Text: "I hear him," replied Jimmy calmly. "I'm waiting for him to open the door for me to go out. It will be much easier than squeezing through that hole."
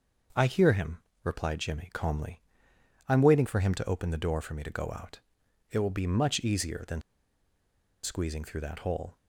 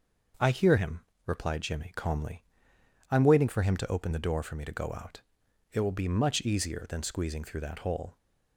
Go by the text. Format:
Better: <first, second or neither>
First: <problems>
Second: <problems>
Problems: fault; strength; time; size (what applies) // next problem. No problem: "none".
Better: second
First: starts louder than the rest; noticeable; until 1.6 s; 6 dB // pauses between "than" and "squeezing"; at 7.0 s; 1.0 s long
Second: starts louder than the rest; noticeable; until 1.6 s; 6 dB